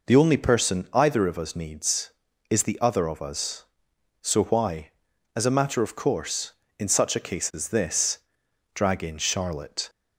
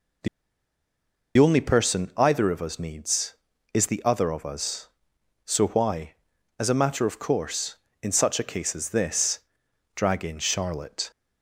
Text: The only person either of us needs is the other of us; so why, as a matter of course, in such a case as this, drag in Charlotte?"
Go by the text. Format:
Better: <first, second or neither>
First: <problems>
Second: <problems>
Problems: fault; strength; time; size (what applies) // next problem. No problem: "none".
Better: first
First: none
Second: pauses between "The" and "only"; at 0.2 s; 1.1 s long